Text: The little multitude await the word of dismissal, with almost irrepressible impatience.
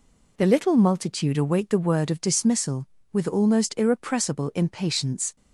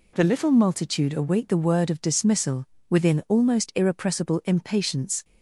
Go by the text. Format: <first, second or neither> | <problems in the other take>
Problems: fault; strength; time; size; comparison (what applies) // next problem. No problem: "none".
first | says "within" for "with"; at 2.8 s